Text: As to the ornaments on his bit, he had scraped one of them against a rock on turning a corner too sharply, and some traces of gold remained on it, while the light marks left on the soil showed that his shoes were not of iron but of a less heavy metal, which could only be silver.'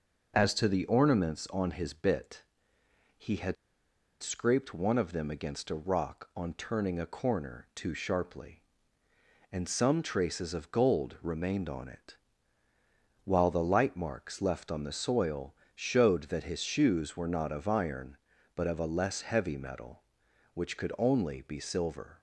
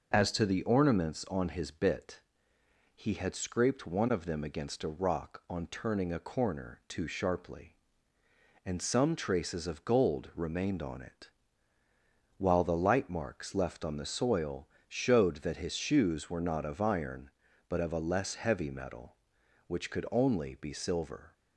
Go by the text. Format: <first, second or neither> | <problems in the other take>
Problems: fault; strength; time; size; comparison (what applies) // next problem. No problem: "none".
second | pauses between "had" and "scraped"; noticeable; at 3.5 s; 0.66 s long // pauses between "soil" and "showed"; slight; at 15.5 s; 0.20 s long; slight in the second